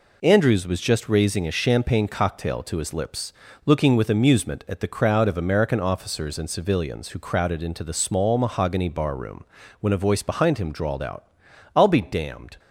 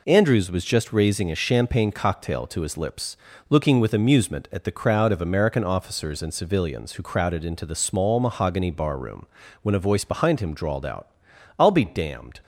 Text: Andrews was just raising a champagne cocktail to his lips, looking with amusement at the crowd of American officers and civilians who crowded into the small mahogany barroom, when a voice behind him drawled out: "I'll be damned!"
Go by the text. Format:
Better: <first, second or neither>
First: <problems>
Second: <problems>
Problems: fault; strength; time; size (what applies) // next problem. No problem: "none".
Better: neither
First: none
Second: none